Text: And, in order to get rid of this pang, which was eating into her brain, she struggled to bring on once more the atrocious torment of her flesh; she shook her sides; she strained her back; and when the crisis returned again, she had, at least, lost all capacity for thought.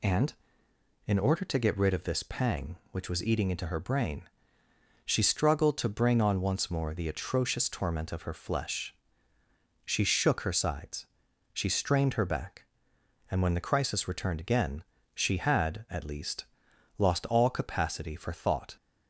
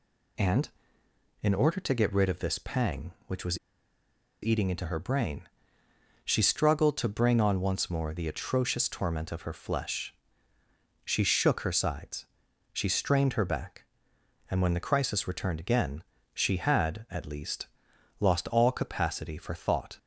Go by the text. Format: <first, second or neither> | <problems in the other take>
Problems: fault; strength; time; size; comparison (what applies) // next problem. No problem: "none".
first | pauses between "was" and "eating"; noticeable; at 3.5 s; 0.84 s long